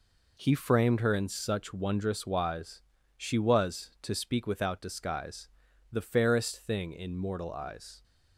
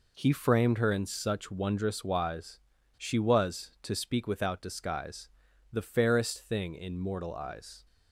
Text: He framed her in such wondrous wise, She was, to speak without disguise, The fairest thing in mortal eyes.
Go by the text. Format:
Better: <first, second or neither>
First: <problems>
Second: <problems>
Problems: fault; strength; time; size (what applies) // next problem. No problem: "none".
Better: neither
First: none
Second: none